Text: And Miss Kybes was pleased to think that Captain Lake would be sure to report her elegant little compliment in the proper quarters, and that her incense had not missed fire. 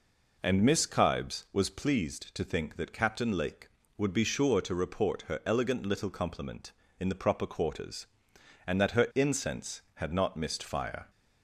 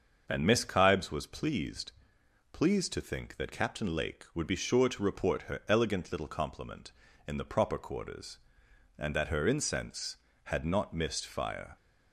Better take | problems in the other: first | starts louder than the rest; until 1.2 s; 6.5 dB // says "pleased" twice; at 2.5 s

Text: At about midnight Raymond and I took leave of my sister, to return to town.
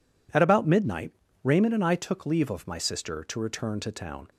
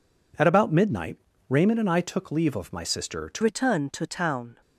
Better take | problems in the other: first | pauses between "midnight" and "Raymond"; slight; at 1.1 s; 0.32 s long; slight in the first // changes voice at "return"; from 3.4 s on; 1.2 s long

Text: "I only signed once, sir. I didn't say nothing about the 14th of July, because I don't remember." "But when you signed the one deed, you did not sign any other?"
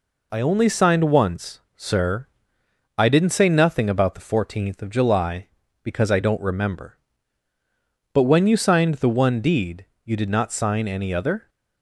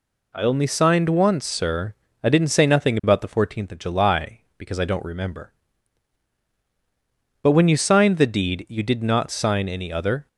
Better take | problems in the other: first | skips "one"; at 8.2 s

